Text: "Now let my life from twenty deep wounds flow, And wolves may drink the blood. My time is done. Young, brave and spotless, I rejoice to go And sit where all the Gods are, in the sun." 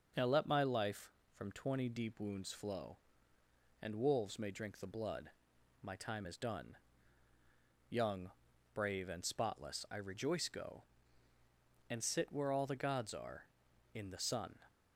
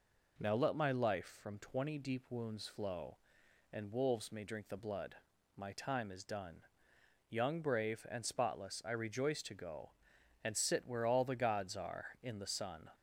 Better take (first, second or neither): second